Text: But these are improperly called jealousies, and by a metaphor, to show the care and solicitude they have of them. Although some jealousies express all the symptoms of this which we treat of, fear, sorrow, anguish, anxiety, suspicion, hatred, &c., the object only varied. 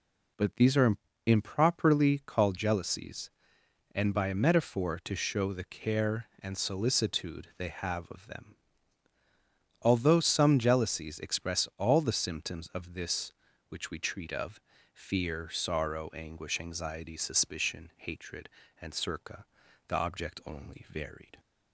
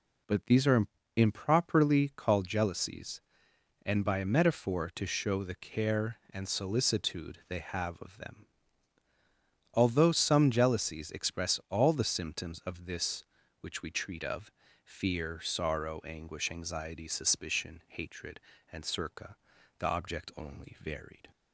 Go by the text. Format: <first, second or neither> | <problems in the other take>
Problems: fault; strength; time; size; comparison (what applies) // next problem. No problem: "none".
neither | pauses between "are" and "improperly"; slight; the same in both